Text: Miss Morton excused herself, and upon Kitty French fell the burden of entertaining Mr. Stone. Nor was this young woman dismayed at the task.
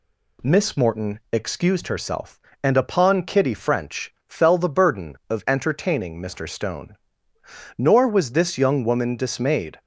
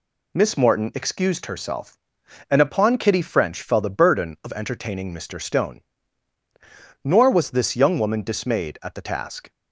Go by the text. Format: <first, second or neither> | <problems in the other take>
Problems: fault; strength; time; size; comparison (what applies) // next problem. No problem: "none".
second | stops before "at the task"; at 9.7 s